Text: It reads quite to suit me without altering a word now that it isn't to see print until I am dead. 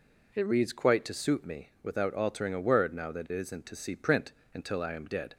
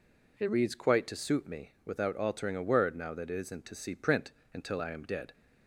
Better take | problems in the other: neither | pauses between "print" and "until"; slight; the same in both

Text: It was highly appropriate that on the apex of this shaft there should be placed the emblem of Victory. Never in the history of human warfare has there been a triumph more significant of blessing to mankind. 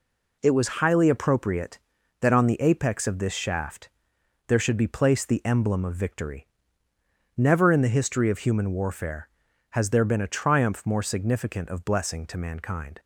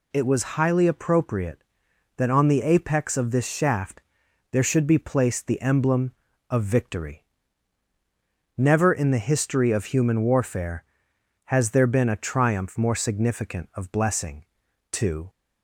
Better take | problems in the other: first | pauses between "shaft" and "there"; noticeable; at 4.0 s; 0.50 s long; noticeable in the first // stops before "mankind"; at 15.2 s

